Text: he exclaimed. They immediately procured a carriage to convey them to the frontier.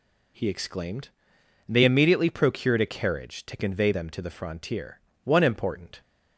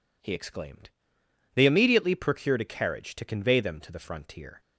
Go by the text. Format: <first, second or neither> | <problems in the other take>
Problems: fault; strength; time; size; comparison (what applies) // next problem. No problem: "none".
second | goes on to say "One important"; noticeable; from 5.2 s on; 0.76 s long